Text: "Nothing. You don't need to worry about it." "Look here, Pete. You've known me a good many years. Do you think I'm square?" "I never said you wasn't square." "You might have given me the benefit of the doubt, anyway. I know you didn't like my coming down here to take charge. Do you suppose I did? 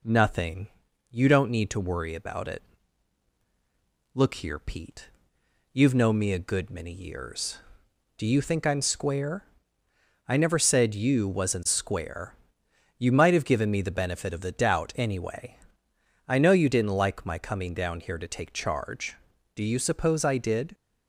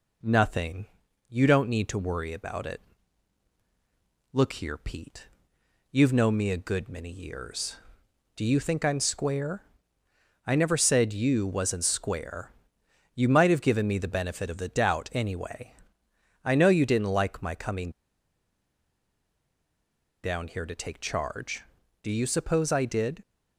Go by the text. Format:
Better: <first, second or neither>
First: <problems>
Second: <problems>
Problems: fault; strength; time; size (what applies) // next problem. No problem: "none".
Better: first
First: none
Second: pauses between "coming" and "down"; strong; at 17.9 s; 2.3 s long